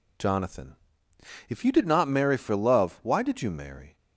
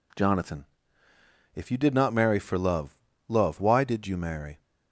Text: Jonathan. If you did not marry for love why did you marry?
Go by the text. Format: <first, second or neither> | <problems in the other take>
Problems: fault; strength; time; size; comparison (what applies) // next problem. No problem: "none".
first | says "love" twice; at 3.2 s